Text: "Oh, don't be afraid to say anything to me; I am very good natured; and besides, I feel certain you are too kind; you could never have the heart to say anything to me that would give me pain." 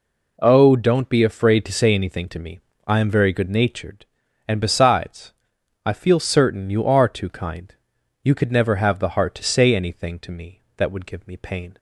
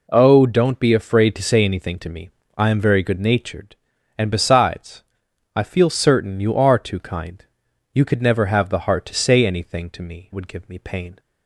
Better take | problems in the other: first | skips "that"; at 10.3 s

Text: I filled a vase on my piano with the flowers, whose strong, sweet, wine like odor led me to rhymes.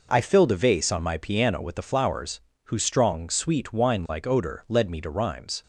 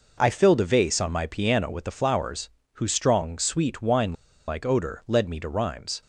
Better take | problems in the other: first | pauses between "wine" and "like"; slight; at 4.1 s; 0.35 s long

